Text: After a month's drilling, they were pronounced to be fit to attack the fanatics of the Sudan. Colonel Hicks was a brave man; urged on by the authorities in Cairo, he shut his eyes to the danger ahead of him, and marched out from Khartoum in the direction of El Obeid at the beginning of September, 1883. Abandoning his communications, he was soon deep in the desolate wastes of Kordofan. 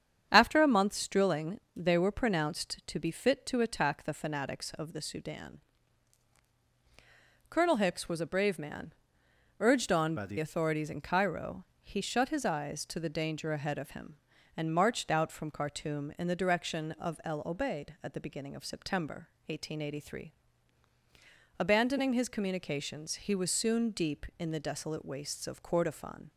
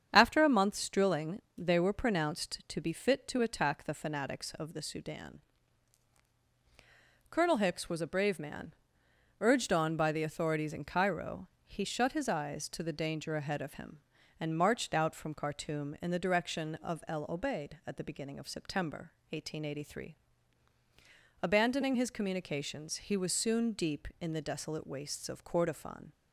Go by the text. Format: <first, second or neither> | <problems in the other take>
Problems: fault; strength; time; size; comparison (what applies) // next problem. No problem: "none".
second | starts louder than the rest; strong; until 1.3 s; 8 dB; strong in the second // changes voice from "by" to "the"; from 10.1 to 10.3 s; 0.2 s long